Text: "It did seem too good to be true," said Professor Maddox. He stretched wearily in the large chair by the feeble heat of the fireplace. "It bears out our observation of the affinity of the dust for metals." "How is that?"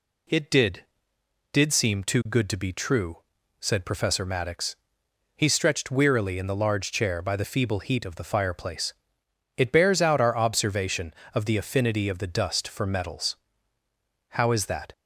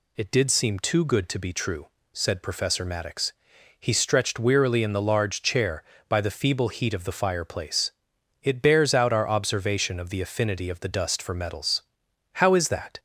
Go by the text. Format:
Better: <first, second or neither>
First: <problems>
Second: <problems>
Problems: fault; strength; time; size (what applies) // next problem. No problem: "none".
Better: second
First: says "did" twice; at 1.5 s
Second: none